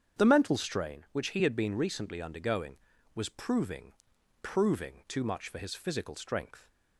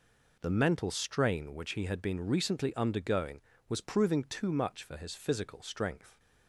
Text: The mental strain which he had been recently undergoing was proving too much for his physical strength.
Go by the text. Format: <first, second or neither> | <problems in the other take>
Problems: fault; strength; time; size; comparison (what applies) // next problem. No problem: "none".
second | starts louder than the rest; strong; until 1.2 s; 8 dB // says "proving" twice; at 4.4 s